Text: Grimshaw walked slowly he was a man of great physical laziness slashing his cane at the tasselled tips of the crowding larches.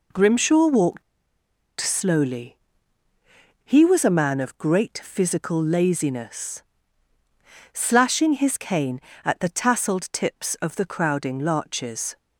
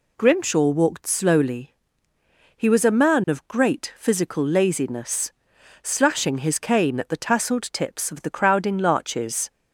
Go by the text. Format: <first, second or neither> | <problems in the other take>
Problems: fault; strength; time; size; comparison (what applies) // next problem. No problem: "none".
second | pauses between "walked" and "slowly"; noticeable; at 1.0 s; 0.78 s long // pauses between "slowly" and "he"; at 2.5 s; 1.1 s long; noticeable in the second // pauses between "laziness" and "slashing"; at 6.6 s; 1.1 s long; noticeable in the second